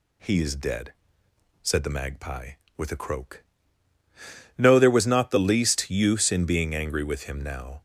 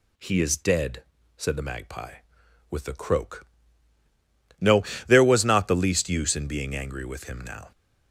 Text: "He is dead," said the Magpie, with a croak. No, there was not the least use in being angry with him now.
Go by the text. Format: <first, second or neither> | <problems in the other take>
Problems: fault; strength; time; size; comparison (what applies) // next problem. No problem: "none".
neither | none